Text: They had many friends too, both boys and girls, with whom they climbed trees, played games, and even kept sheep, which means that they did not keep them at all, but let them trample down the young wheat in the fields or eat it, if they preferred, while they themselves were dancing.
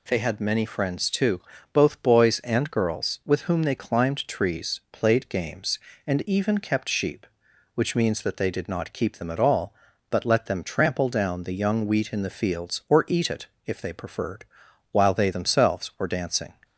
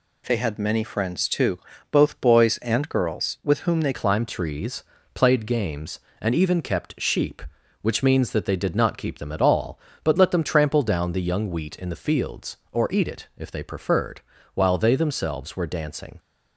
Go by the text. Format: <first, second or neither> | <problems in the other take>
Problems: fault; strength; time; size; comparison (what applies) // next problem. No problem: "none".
first | changes voice at "climbed"; from 3.9 s on; 12.2 s long